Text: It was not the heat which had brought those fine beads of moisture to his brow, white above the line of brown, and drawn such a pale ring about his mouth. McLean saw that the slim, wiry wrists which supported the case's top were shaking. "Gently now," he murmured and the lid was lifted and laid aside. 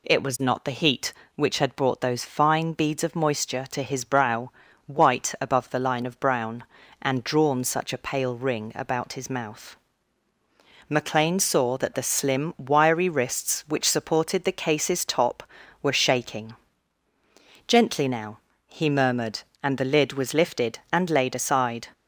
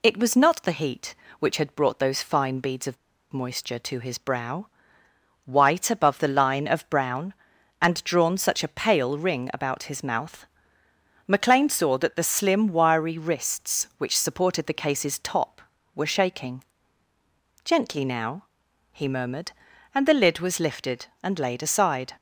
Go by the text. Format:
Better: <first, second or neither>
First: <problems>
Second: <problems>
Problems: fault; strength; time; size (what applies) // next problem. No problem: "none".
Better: first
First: none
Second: pauses between "of" and "moisture"; slight; at 2.9 s; 0.35 s long